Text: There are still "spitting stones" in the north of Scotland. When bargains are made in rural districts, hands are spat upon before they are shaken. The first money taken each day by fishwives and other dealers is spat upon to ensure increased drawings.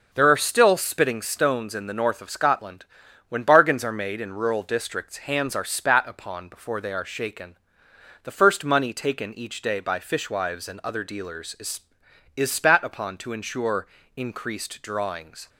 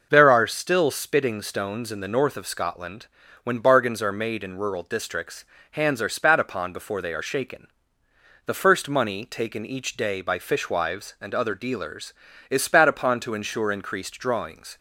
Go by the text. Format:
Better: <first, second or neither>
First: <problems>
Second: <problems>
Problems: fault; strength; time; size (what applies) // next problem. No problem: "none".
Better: second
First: starts louder than the rest; noticeable; until 1.1 s; 6 dB // says "is" twice; at 12.3 s // pauses between "ensure" and "increased"; slight; at 13.8 s; 0.30 s long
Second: none